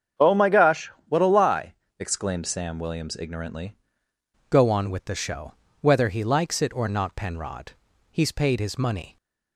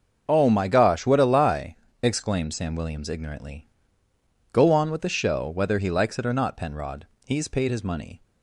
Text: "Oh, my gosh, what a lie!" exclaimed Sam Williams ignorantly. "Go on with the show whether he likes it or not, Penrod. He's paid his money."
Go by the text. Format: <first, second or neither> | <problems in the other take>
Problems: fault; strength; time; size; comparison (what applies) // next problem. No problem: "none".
second | starts louder than the rest; strong; until 1.3 s; 8 dB; also in the second // changes voice at "Go"; from 4.5 s on; 4.6 s long // pauses between "show" and "whether"; slight; at 5.5 s; 0.28 s long